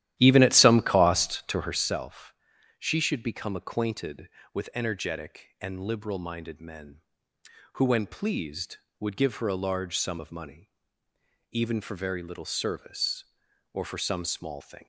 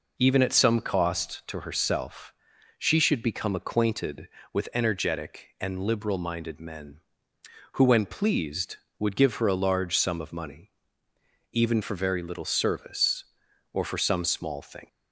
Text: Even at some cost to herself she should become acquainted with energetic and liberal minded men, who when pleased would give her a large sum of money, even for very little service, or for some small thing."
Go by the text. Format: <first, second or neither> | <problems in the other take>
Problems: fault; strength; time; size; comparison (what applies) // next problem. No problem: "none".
second | starts louder than the rest; strong; until 2.0 s; 13 dB // pauses between "herself" and "she"; at 2.3 s; 0.44 s long; also in the second